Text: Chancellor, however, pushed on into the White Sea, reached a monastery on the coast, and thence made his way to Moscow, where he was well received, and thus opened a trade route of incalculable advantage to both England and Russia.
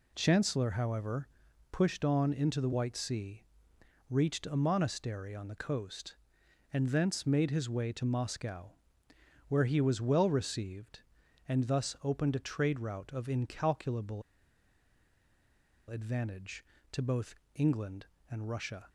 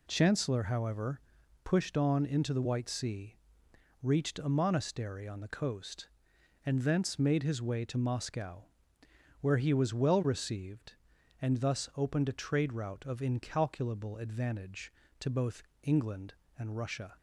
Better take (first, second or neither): second